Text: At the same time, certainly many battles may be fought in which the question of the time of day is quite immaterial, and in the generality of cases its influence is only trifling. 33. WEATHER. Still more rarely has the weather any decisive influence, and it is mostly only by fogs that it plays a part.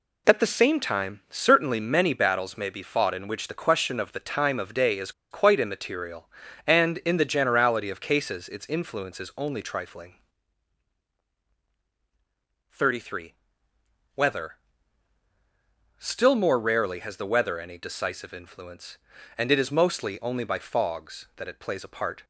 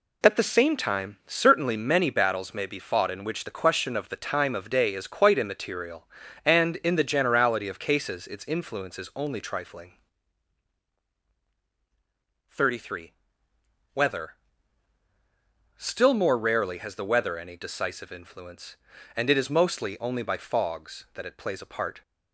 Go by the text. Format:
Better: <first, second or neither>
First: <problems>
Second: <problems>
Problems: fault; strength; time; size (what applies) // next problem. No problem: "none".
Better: second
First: pauses between "is" and "quite"; slight; at 5.1 s; 0.20 s long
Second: none